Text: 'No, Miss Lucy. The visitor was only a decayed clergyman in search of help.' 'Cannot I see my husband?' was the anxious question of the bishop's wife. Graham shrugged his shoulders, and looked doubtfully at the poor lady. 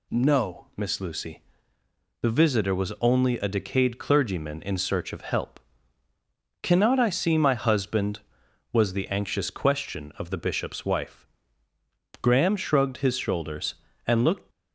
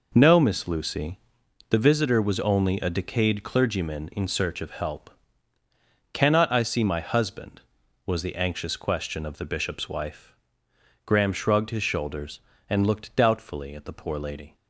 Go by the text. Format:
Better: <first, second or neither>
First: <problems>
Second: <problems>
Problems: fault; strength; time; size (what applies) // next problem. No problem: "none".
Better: second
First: stops before "doubtfully at the poor lady"; at 14.5 s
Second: none